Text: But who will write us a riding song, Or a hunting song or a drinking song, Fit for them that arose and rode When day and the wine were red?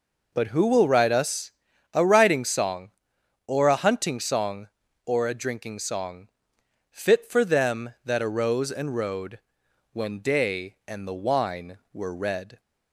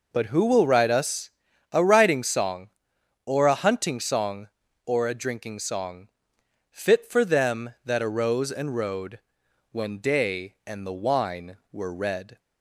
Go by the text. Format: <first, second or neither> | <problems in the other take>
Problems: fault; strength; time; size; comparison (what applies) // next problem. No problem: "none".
neither | pauses between "us" and "a"; the same in both // pauses between "rode" and "When"; noticeable; the same in both